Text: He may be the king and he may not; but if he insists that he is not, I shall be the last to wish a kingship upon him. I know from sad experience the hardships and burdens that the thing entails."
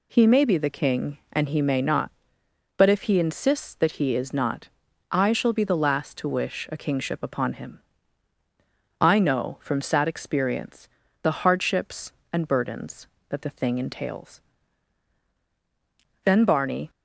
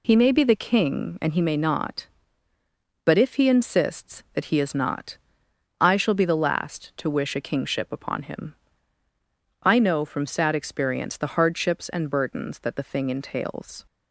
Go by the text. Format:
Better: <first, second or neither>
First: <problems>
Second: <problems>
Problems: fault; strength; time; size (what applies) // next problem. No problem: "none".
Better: second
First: pauses between "experience" and "the"; slight; at 10.8 s; 0.34 s long // goes on to say "Then Barney"; noticeable; from 16.2 s on; 0.66 s long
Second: none